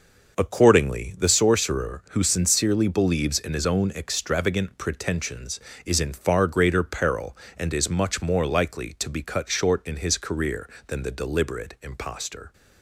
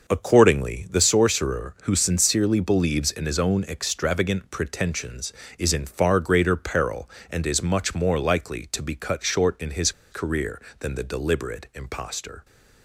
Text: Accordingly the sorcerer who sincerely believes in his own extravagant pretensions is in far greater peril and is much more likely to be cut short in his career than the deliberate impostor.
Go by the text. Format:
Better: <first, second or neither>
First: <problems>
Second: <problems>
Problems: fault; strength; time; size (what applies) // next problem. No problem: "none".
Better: first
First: none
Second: pauses between "his" and "career"; slight; at 9.9 s; 0.20 s long